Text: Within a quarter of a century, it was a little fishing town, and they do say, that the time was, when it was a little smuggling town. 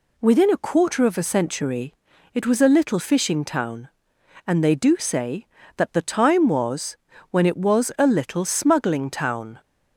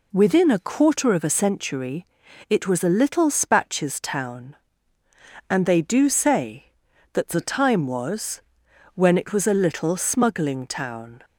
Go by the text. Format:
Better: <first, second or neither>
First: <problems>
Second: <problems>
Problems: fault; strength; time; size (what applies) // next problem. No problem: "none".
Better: first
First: none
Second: says "spatches" for "fishing"; at 3.3 s